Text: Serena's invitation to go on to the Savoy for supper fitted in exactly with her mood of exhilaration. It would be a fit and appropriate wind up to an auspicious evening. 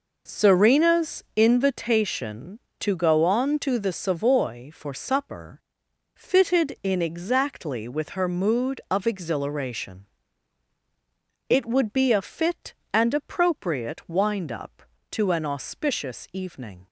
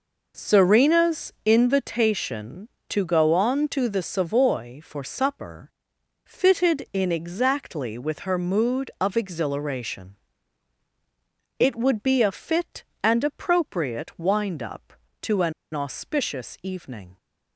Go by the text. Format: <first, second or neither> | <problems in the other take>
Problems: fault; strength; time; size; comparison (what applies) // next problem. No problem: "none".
first | pauses between "supper" and "fitted"; noticeable; at 5.7 s; 0.54 s long; noticeable in the first // pauses between "an" and "auspicious"; slight; at 15.5 s; 0.22 s long